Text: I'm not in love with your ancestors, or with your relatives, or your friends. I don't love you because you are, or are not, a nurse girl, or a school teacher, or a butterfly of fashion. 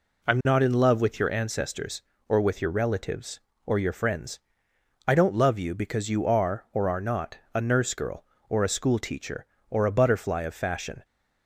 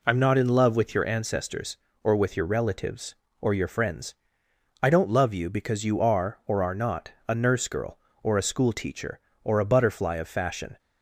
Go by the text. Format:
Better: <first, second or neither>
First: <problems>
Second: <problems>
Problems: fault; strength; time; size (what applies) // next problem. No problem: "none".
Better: neither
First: none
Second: none